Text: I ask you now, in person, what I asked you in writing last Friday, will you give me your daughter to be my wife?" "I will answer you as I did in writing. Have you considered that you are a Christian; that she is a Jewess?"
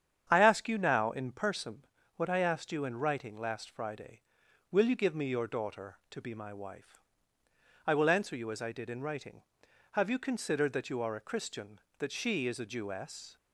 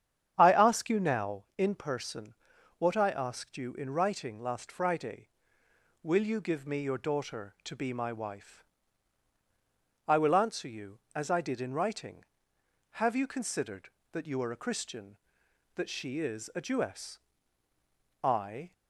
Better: first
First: starts louder than the rest; strong; until 1.2 s; 8.5 dB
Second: starts louder than the rest; strong; until 1.3 s; 8.5 dB // goes on to say "I"; slight; from 18.2 s on; 0.48 s long

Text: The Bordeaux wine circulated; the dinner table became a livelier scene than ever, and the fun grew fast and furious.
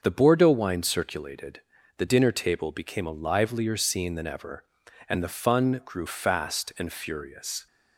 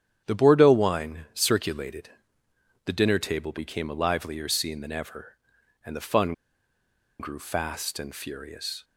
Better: first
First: starts louder than the rest; until 1.0 s; 6.5 dB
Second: starts louder than the rest; strong; until 1.2 s; 9 dB // pauses between "fun" and "grew"; noticeable; at 6.3 s; 0.87 s long

